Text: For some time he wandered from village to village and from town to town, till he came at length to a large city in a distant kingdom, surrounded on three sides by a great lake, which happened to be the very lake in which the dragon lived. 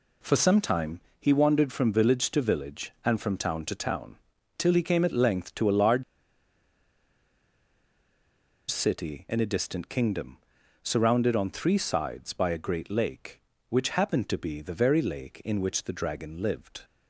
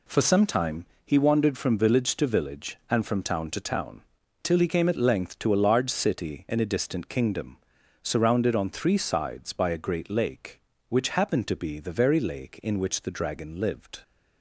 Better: second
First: pauses between "time" and "he"; slight; at 0.9 s; 0.20 s long // pauses between "large" and "city"; strong; at 6.0 s; 2.6 s long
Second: pauses between "time" and "he"; slight; at 0.8 s; 0.20 s long

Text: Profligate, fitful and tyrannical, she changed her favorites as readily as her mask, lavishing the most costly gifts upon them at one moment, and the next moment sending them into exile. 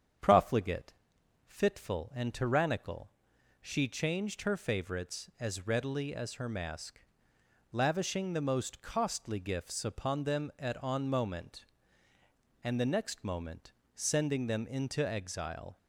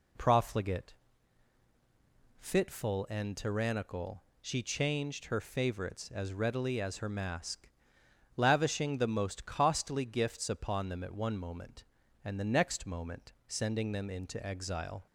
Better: second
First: starts louder than the rest; strong; until 1.7 s; 8 dB // says "on" for "one"; at 10.8 s // pauses between "moment" and "sending"; slight; at 13.7 s; 0.22 s long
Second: none

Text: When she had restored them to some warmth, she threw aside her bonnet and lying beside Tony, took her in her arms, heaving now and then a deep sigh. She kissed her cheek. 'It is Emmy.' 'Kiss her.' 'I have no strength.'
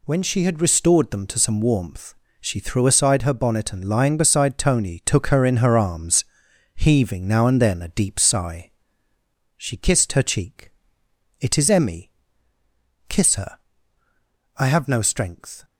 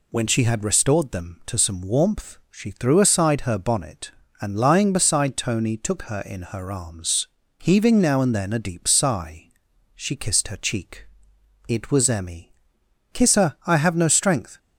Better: first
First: none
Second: says "was" for "is"; at 11.9 s

